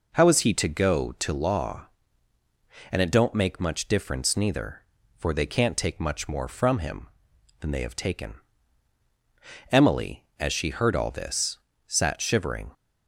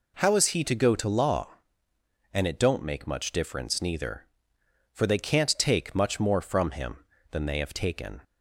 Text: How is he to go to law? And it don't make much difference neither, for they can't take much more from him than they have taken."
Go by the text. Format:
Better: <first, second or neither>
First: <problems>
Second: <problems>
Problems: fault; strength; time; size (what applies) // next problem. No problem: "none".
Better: second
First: goes on to say "Emily as she heard all this sat shivering"; strong; from 9.7 s on; 3.0 s long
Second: none